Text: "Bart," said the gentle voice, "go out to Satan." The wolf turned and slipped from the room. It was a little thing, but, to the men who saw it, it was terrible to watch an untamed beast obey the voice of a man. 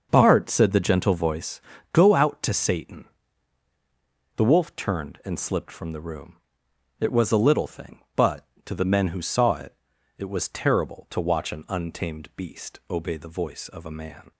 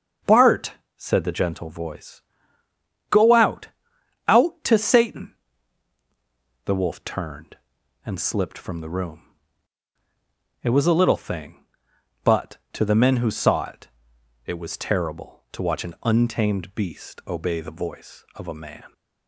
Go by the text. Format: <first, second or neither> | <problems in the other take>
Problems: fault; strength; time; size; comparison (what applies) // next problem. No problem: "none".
first | starts louder than the rest; until 1.4 s; 6.5 dB; also in the first // says "out" twice; at 4.2 s